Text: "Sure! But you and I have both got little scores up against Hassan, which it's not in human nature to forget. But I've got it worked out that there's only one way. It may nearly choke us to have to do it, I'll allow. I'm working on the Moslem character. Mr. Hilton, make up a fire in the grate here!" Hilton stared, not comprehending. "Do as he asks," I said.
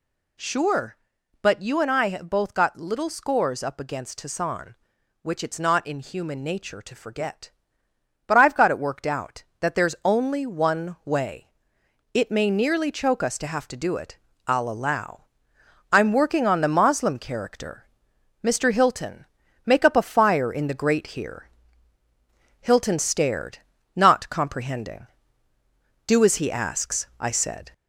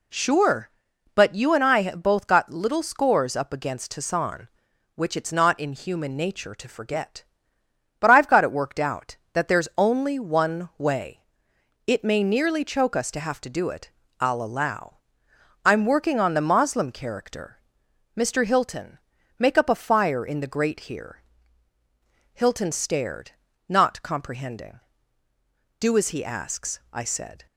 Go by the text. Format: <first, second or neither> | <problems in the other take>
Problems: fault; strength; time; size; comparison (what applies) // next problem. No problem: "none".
second | gets louder; throughout; 3.5 dB